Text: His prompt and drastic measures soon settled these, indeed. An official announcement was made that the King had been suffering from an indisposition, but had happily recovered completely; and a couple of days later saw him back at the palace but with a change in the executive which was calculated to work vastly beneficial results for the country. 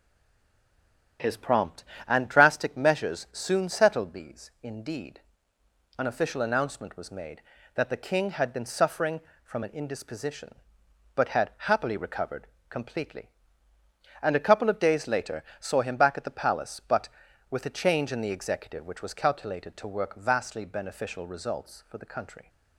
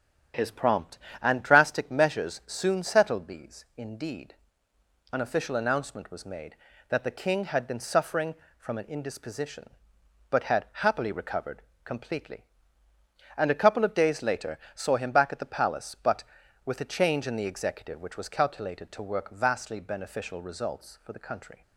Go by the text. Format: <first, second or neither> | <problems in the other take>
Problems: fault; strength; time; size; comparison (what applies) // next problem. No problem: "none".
second | stays silent before the first word; noticeable; until 1.1 s; 1.1 s long // starts louder than the rest; strong; until 2.4 s; 8 dB; strong in the second // pauses between "had" and "happily"; slight; at 11.5 s; 0.18 s long; slight in the second // pauses between "recovered" and "completely"; slight; at 12.4 s; 0.24 s long; slight in the second // pauses between "later" and "saw"; slight; at 15.4 s; 0.16 s long; slight in the second